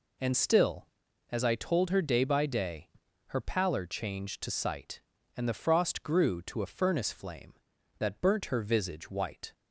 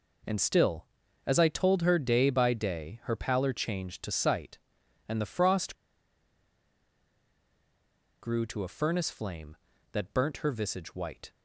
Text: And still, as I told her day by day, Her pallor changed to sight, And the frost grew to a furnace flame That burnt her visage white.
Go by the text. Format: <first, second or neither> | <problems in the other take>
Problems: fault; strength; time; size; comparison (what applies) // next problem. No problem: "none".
first | pauses between "frost" and "grew"; strong; at 5.7 s; 2.4 s long